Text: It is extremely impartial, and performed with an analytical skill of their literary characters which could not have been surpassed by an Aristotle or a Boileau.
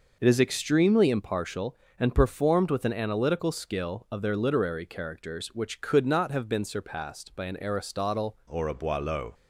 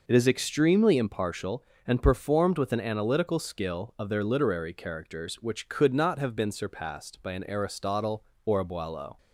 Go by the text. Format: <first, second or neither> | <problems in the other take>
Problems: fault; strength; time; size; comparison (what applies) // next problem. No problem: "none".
second | changes voice at "or"; from 8.5 s on; 0.8 s long